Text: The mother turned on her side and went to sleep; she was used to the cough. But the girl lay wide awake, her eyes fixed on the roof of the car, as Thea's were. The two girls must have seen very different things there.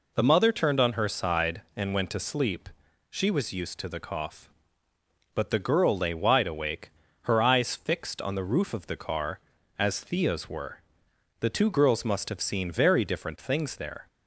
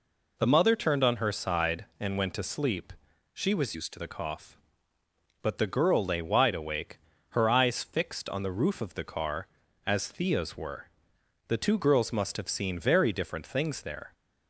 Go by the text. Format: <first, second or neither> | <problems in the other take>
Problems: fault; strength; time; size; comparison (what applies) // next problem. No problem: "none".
first | changes voice from "used" to "to"; from 3.7 to 3.9 s; 0.2 s long